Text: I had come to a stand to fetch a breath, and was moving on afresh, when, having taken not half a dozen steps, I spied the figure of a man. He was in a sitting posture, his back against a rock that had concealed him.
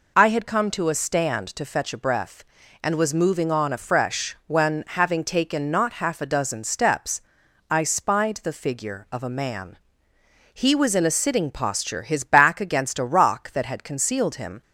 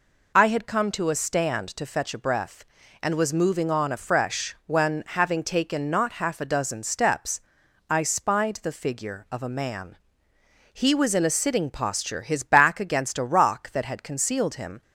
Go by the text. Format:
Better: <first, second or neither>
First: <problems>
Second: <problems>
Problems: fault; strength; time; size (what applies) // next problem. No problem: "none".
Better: neither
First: none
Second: none